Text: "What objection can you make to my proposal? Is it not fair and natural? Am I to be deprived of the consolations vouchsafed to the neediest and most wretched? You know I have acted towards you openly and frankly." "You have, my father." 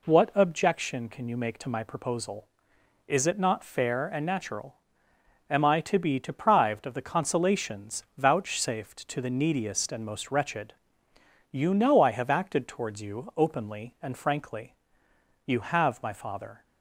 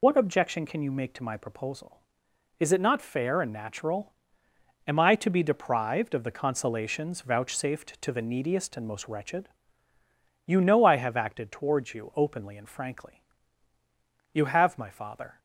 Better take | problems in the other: first | loses the start of "What"; at 0.0 s; 85 ms

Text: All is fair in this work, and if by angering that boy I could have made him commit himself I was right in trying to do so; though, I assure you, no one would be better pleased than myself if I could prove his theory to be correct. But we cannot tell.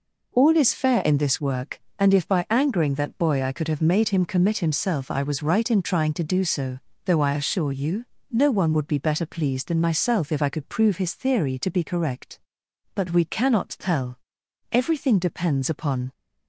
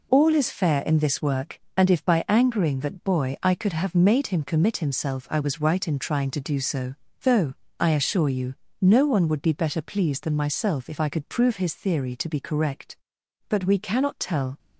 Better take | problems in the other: second | goes on to say "Everything depends upon"; from 14.7 s on; 1.4 s long

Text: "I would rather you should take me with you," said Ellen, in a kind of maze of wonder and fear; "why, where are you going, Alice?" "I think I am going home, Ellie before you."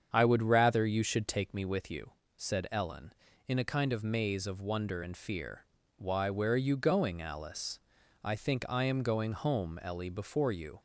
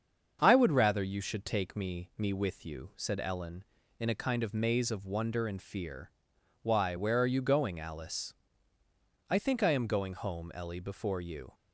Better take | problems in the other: first | starts louder than the rest; until 1.4 s; 7 dB; strong in the first // says "me" twice; at 2.1 s

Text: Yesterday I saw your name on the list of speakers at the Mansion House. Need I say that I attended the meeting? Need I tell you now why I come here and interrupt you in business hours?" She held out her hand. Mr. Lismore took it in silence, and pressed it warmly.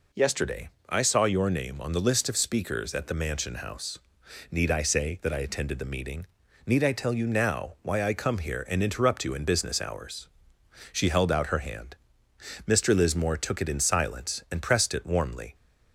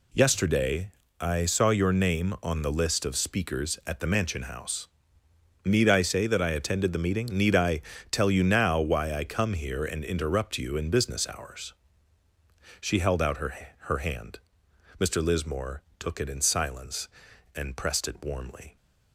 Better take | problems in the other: first | pauses between "Yesterday" and "I"; slight; at 0.9 s; 0.30 s long; slight in the first // pauses between "I" and "tell"; slight; at 7.7 s; 0.30 s long // says "her" twice; at 13.8 s // pauses between "Lismore" and "took"; slight; at 15.8 s; 0.16 s long

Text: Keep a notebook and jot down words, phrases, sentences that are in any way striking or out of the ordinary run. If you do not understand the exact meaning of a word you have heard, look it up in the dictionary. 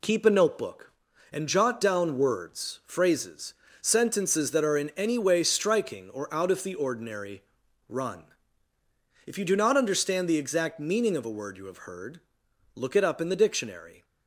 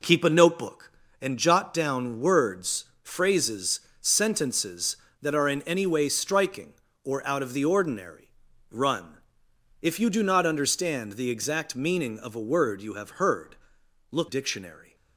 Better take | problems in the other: first | pauses between "ordinary" and "run"; at 8.2 s; 0.44 s long; also in the first // skips "it up in the"; at 14.2 s

